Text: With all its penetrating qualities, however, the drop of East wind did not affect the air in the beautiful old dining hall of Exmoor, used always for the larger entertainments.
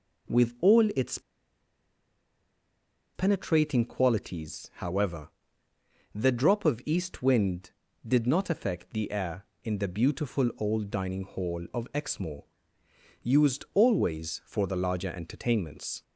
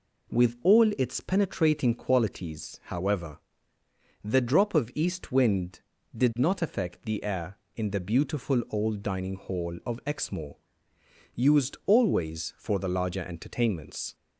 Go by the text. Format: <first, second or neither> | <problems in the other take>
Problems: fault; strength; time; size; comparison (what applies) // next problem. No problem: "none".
second | pauses between "its" and "penetrating"; strong; at 1.1 s; 1.9 s long